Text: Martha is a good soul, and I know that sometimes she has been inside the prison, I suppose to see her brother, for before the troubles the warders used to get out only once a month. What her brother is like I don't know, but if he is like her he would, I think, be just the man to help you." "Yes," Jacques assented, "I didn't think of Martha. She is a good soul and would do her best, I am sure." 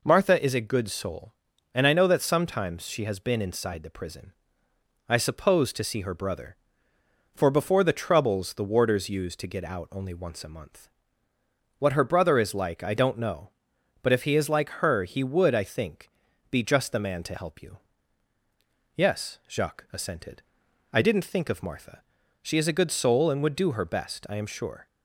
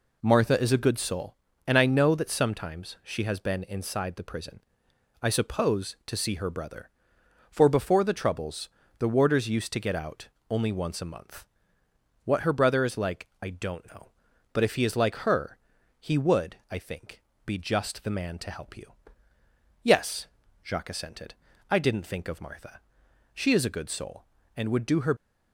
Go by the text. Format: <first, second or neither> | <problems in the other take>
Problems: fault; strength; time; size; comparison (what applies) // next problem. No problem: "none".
first | pauses between "troubles" and "the"; slight; at 8.6 s; 0.30 s long // pauses between "out" and "only"; slight; at 10.2 s; 0.22 s long // pauses between "her" and "he"; noticeable; at 15.5 s; 0.46 s long // stops before "best I am sure"; at 25.1 s